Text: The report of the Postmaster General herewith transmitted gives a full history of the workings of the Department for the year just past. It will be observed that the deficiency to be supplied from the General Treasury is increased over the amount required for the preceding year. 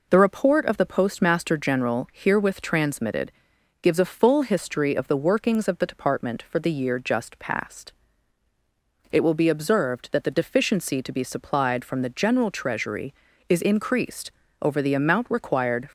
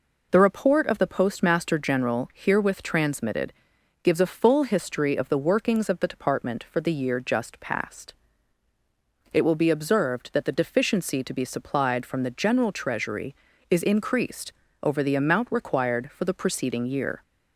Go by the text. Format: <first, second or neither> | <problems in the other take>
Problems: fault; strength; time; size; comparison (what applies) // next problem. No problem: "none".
second | pauses between "transmitted" and "gives"; noticeable; at 3.3 s; 0.48 s long; noticeable in the second // pauses between "increased" and "over"; slight; at 14.3 s; 0.30 s long; slight in the second // stops before "for the preceding year"; at 15.8 s